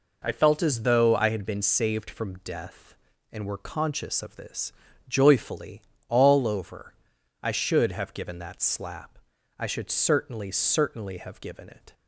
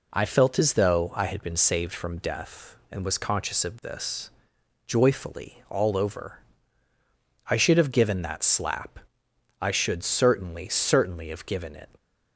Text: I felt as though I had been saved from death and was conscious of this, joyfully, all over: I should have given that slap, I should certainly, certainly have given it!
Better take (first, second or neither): second